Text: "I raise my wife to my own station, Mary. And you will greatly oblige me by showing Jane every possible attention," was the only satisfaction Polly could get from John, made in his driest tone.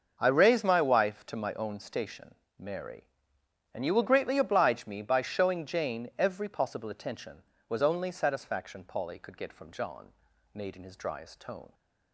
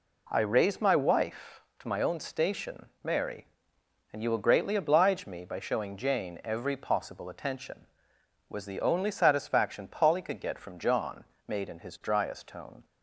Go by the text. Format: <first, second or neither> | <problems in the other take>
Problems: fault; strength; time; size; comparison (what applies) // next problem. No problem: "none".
second | starts louder than the rest; noticeable; until 1.2 s; 6 dB // skips "the"; at 7.8 s